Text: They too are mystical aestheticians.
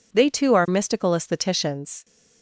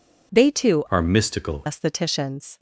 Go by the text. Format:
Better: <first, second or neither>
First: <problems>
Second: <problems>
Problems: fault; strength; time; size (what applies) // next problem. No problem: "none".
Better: first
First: none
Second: changes voice from "are" to "mystical"; from 0.9 to 1.6 s; 0.7 s long